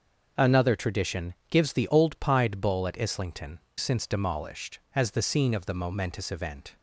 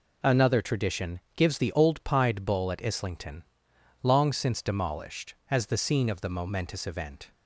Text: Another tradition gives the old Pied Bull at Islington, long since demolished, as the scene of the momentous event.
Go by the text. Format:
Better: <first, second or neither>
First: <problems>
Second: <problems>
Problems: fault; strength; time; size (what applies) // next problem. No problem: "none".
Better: second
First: starts louder than the rest; noticeable; until 1.5 s; 6 dB // pauses between "tradition" and "gives"; slight; at 1.3 s; 0.16 s long // skips "long"; at 3.6 s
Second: pauses between "tradition" and "gives"; slight; at 1.1 s; 0.16 s long